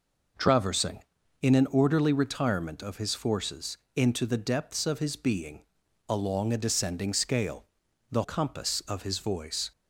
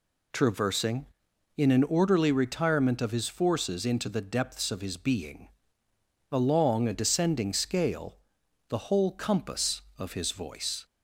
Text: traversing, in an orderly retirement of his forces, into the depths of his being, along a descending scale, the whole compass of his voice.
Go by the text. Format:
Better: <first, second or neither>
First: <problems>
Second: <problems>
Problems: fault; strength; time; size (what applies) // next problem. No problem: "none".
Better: second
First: skips "whole"; at 8.2 s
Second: none